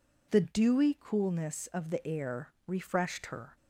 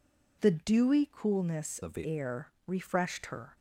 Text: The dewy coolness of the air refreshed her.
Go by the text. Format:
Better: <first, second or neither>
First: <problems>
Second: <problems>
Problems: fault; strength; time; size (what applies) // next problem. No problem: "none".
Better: first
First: pauses between "air" and "refreshed"; slight; at 2.5 s; 0.15 s long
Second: changes voice from "of" to "the"; from 1.8 to 2.0 s; 0.2 s long // pauses between "air" and "refreshed"; slight; at 2.4 s; 0.16 s long